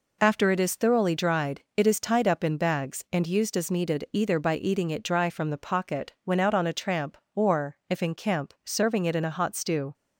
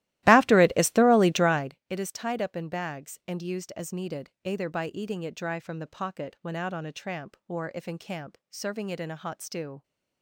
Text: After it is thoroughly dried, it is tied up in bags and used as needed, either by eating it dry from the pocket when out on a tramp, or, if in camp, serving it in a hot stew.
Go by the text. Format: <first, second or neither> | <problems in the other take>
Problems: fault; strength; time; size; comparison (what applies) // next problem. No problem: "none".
first | starts louder than the rest; strong; until 1.8 s; 16.5 dB